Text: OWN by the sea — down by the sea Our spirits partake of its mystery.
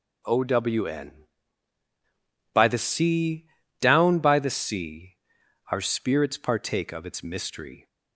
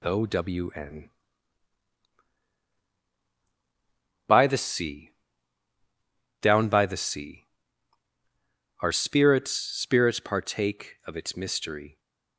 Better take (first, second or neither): first